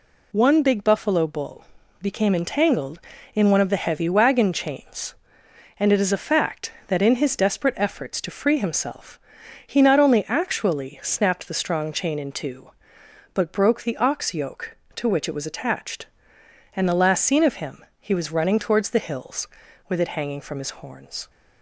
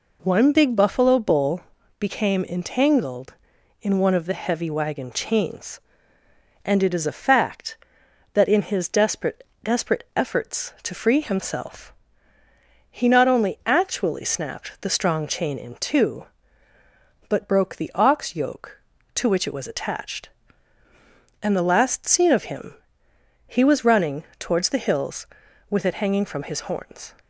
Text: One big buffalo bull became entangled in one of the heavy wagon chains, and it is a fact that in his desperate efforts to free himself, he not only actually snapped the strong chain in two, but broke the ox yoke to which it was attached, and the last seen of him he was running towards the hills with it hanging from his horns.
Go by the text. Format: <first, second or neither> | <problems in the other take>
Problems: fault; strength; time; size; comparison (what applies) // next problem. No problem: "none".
first | pauses between "bull" and "became"; at 1.6 s; 0.38 s long; also in the first // says "desperate" twice; at 9.6 s // pauses between "him" and "he"; noticeable; at 22.7 s; 0.72 s long // pauses between "running" and "towards"; slight; at 24.2 s; 0.16 s long